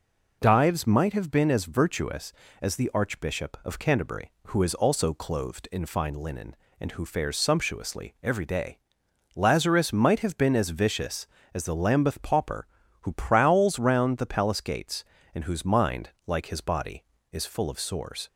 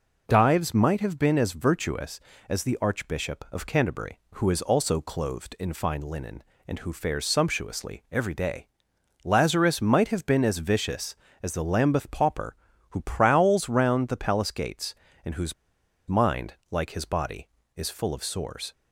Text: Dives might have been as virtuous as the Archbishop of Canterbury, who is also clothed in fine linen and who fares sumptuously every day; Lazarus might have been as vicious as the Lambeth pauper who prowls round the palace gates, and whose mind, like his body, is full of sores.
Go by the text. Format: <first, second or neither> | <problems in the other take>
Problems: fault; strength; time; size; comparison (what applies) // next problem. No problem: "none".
first | pauses between "whose" and "mind"; noticeable; at 15.5 s; 0.53 s long